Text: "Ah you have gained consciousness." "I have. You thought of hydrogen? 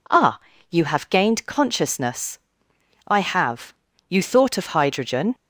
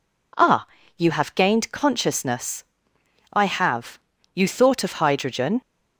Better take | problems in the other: neither | pauses between "Ah" and "you"; slight; the same in both

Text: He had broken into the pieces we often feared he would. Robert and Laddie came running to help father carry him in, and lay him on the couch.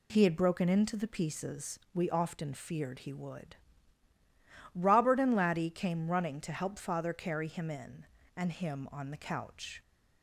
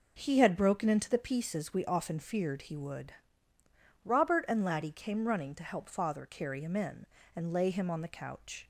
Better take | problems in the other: second | skips "lay"; at 8.5 s

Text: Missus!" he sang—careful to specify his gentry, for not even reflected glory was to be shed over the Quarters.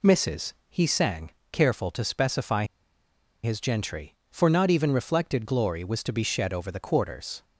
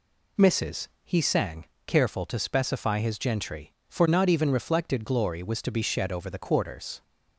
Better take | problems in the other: second | pauses between "specify" and "his"; noticeable; at 2.6 s; 0.78 s long

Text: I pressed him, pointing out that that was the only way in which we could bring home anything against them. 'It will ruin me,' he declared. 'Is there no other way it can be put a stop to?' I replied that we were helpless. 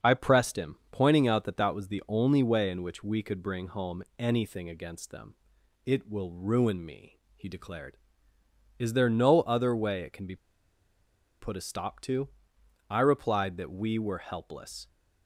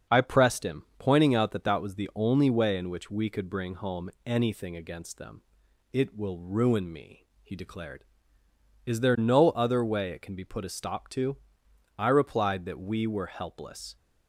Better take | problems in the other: second | starts louder than the rest; until 1.1 s; 7 dB; also in the second // pauses between "home" and "anything"; slight; at 4.0 s; 0.16 s long; slight in the second // pauses between "be" and "put"; at 10.3 s; 1.0 s long

